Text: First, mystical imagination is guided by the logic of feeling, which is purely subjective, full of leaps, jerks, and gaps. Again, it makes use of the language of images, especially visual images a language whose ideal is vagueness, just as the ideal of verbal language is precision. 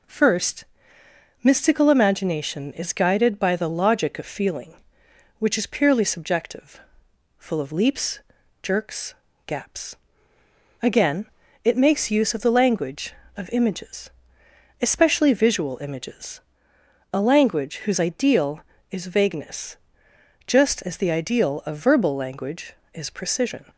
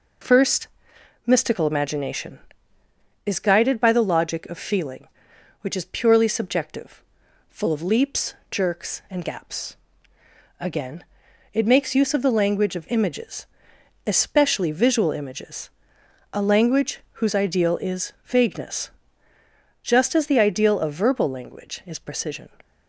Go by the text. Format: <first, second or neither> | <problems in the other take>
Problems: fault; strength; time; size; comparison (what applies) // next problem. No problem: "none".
second | skips "and"; at 9.2 s // pauses between "images" and "a"; noticeable; at 16.3 s; 0.72 s long; noticeable in the second